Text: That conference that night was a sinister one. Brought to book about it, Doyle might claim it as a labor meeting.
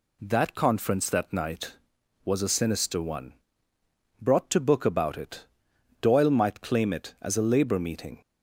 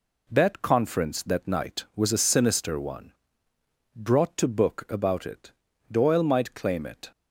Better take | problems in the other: first | stops before "as a labor meeting"; at 7.1 s

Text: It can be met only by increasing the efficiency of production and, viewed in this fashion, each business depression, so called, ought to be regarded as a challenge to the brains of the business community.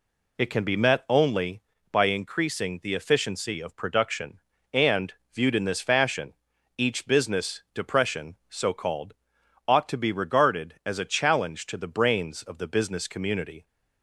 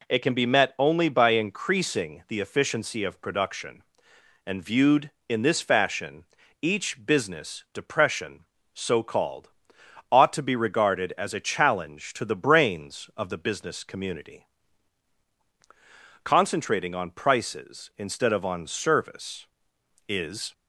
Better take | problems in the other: first | goes on to say "Concentrating on prices instead of on service is"; strong; from 16.2 s on; 4.2 s long

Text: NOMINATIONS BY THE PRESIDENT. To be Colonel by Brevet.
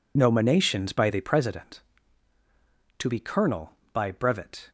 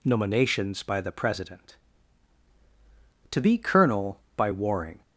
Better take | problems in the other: first | says "Warring" for "Brevet"; at 4.5 s

